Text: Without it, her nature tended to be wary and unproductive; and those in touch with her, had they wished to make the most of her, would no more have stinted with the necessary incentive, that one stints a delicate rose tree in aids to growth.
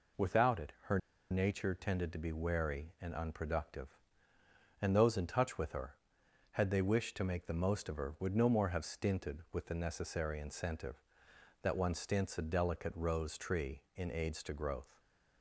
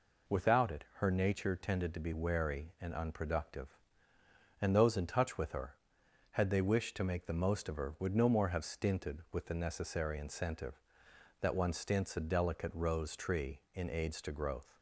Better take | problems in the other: second | pauses between "her" and "nature"; slight; at 0.9 s; 0.31 s long

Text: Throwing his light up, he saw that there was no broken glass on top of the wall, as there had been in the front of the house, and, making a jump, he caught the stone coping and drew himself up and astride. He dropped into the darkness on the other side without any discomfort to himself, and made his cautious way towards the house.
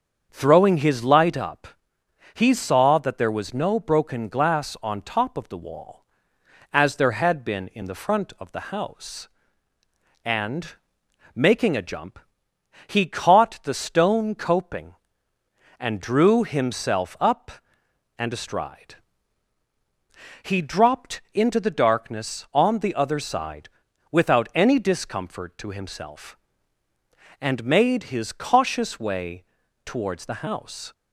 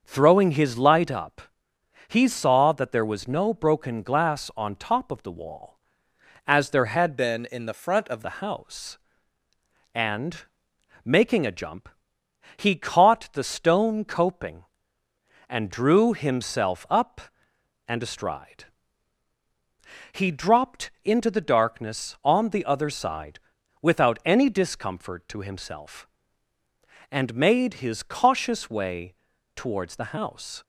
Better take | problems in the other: first | starts louder than the rest; until 1.0 s; 7 dB; strong in the first // changes voice from "been" to "of"; from 7.1 to 8.2 s; 1.1 s long // pauses between "side" and "without"; at 23.3 s; 0.44 s long; also in the first // pauses between "way" and "towards"; at 29.1 s; 0.40 s long; also in the first

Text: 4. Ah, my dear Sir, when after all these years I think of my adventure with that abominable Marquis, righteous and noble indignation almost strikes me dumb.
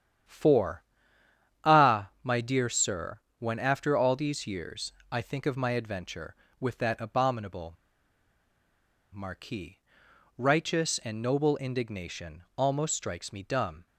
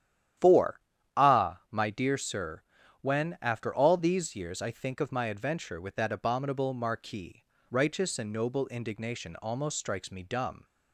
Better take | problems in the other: second | starts louder than the rest; strong; until 2.0 s; 9.5 dB; strong in the second // pauses between "years" and "I"; slight; at 4.9 s; 0.18 s long // pauses between "abominable" and "Marquis"; strong; at 7.7 s; 1.4 s long

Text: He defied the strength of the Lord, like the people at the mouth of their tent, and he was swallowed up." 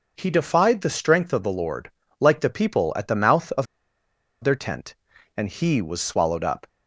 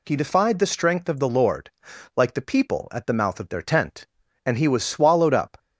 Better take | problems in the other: second | pauses between "of" and "their"; noticeable; at 3.6 s; 0.77 s long

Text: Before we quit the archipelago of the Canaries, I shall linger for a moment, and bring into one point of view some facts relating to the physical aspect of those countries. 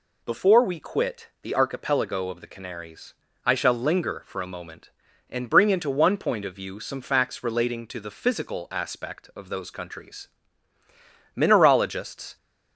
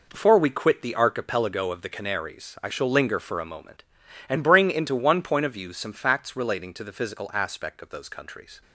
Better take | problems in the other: second | goes on to say "Mineralogists"; noticeable; from 11.3 s on; 1.0 s long

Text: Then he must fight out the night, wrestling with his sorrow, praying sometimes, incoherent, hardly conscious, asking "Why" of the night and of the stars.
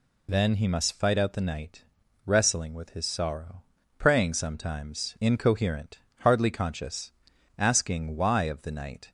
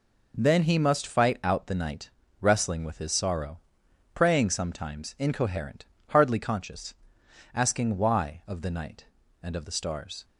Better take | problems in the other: second | stops before "and of the stars"; at 9.0 s

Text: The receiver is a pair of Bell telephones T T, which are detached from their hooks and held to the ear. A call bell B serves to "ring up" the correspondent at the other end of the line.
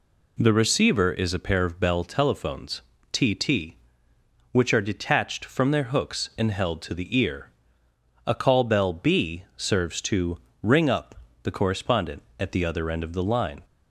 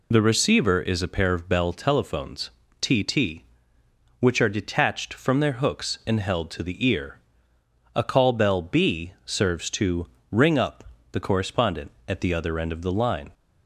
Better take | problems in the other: first | loses the start of "The"; at 0.1 s; 45 ms // pauses between "telephones" and "T"; slight; at 2.5 s; 0.30 s long; slight in the first // pauses between "to" and "ring"; slight; at 10.0 s; 0.24 s long; slight in the first // pauses between "up" and "the"; slight; at 10.8 s; 0.28 s long; slight in the first

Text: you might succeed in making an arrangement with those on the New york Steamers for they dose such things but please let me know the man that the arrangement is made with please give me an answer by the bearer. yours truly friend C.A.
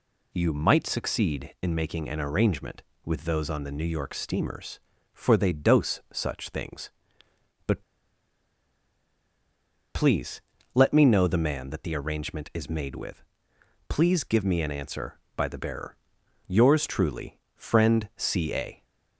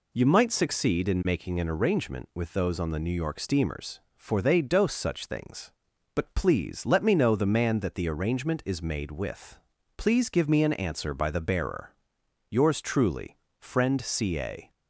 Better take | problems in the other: second | pauses between "but" and "please"; strong; at 7.8 s; 2.1 s long // pauses between "please" and "let"; slight; at 10.4 s; 0.32 s long // pauses between "with" and "please"; noticeable; at 13.2 s; 0.64 s long; also in the second // pauses between "truly" and "friend"; slight; at 17.3 s; 0.18 s long; slight in the second

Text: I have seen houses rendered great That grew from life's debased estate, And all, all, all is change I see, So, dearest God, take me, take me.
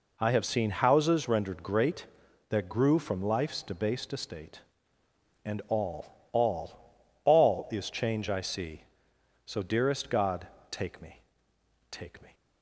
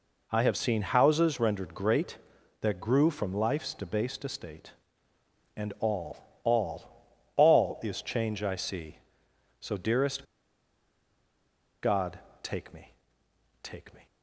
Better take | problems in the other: first | pauses between "dearest" and "God"; strong; at 10.2 s; 1.5 s long

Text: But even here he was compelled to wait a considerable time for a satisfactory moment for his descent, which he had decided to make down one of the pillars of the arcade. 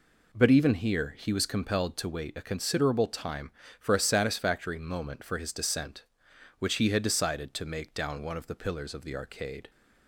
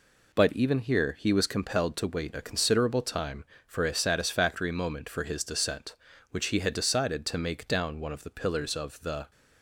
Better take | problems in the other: first | stops before "arcade"; at 9.3 s

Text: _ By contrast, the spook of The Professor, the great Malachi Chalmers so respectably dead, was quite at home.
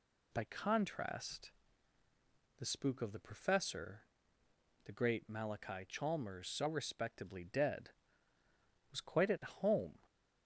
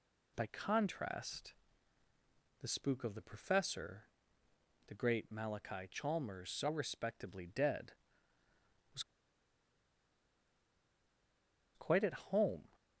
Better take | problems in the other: first | pauses between "was" and "quite"; strong; at 9.0 s; 2.7 s long

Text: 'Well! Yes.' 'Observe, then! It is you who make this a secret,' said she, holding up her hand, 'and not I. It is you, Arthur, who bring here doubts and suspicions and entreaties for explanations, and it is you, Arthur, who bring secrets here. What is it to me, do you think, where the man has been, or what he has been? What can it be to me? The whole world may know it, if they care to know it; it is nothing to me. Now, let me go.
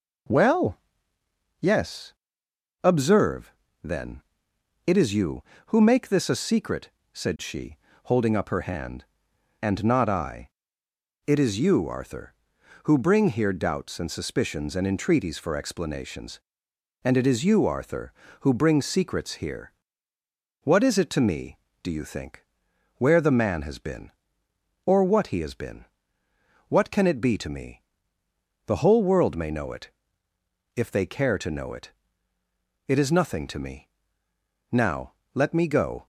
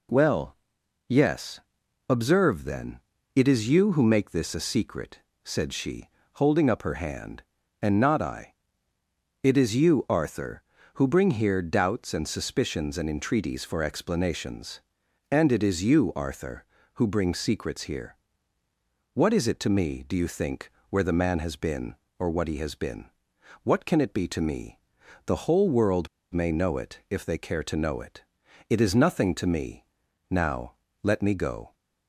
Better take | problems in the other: first | pauses between "world" and "may"; slight; at 26.0 s; 0.25 s long

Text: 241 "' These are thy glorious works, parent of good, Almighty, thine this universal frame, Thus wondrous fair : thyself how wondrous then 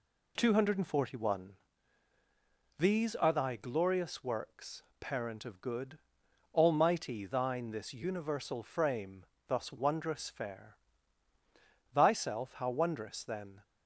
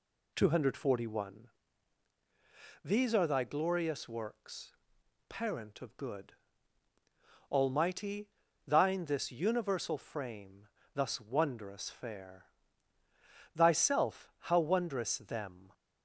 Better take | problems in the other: first | says "them" for "then"; at 15.1 s

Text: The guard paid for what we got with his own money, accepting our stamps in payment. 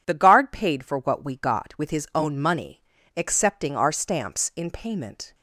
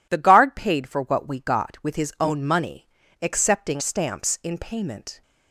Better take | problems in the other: first | skips "our"; at 3.8 s

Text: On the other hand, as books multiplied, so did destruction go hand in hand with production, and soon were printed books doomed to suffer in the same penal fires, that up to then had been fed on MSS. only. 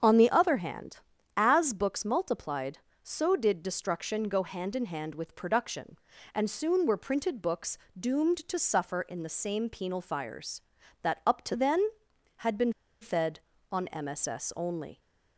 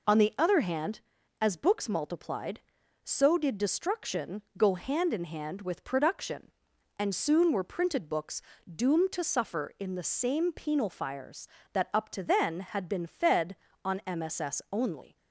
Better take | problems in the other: second | starts louder than the rest; strong; until 1.4 s; 7.5 dB // pauses between "books" and "doomed"; slight; at 7.7 s; 0.22 s long; slight in the second // pauses between "been" and "fed"; slight; at 12.7 s; 0.29 s long

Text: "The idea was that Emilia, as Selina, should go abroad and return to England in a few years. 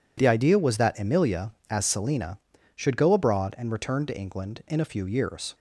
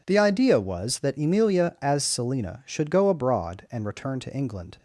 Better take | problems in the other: first | stops before "in a few years"; at 4.7 s

